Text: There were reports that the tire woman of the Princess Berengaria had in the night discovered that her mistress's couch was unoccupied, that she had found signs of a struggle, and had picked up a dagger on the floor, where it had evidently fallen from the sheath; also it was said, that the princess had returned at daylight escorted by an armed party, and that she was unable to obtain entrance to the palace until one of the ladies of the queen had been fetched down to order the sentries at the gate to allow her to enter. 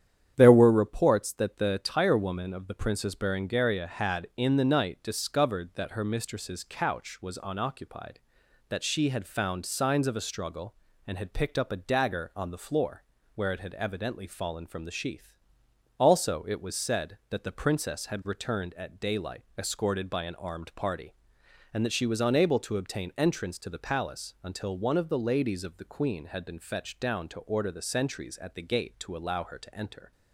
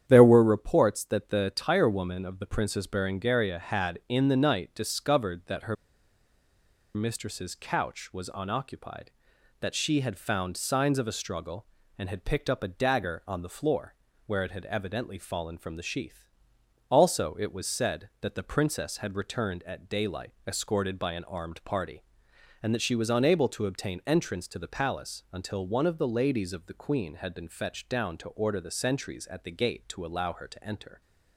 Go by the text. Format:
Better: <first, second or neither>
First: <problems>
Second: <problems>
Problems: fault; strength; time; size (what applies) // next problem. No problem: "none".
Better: first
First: starts louder than the rest; strong; until 1.3 s; 9.5 dB // pauses between "daylight" and "escorted"; slight; at 19.4 s; 0.16 s long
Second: starts louder than the rest; strong; until 1.0 s; 9.5 dB // pauses between "her" and "mistress's"; at 5.7 s; 1.2 s long // pauses between "daylight" and "escorted"; slight; at 20.3 s; 0.16 s long